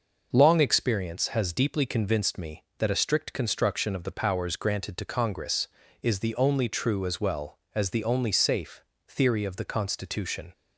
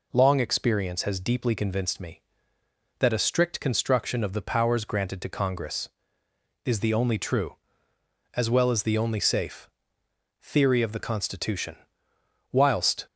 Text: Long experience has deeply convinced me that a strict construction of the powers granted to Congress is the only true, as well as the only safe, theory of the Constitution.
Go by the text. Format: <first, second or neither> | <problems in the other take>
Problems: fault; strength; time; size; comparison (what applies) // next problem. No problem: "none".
first | goes on to say "Whilst"; from 12.5 s on; 0.56 s long